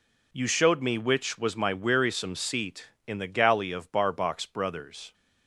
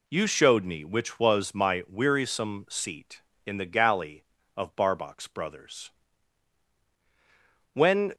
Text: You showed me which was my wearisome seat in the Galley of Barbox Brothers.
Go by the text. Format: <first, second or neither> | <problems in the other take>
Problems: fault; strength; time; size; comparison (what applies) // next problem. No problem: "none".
first | goes on to say "When"; slight; from 7.7 s on; 0.40 s long